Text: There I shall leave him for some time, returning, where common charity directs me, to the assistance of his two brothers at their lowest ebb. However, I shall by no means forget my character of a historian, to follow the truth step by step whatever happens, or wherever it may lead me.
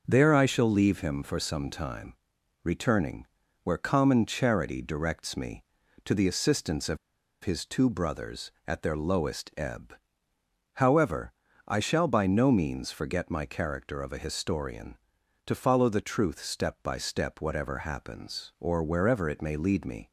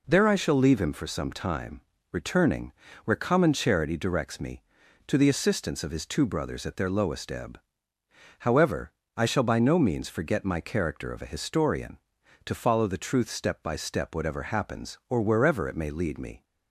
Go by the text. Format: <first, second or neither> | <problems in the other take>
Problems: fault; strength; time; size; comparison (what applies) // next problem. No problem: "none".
second | starts louder than the rest; noticeable; until 1.0 s; 6 dB // pauses between "of" and "his"; noticeable; at 6.9 s; 0.46 s long